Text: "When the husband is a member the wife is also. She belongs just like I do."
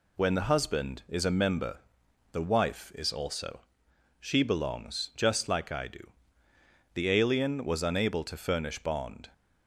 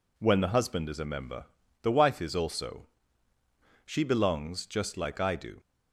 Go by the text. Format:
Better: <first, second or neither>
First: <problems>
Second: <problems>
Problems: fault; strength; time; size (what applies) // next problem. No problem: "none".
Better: second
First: pauses between "member" and "the"; noticeable; at 1.8 s; 0.52 s long // goes on to say "The alien was unable to furnish bond"; strong; from 6.9 s on; 2.3 s long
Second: pauses between "member" and "the"; at 1.4 s; 0.38 s long